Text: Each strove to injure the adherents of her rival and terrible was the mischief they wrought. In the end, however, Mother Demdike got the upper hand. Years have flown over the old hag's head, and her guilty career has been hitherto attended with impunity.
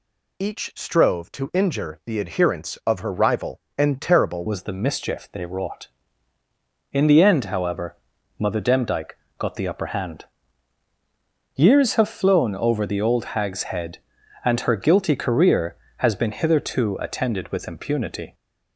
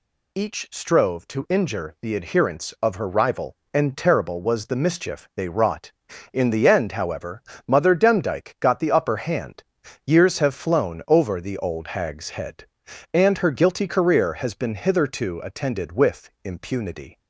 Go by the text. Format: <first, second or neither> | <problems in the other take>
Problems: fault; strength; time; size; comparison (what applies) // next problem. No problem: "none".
second | changes voice at "was"; from 4.4 s on; 13.9 s long // pauses between "Demdike" and "got"; slight; at 9.1 s; 0.20 s long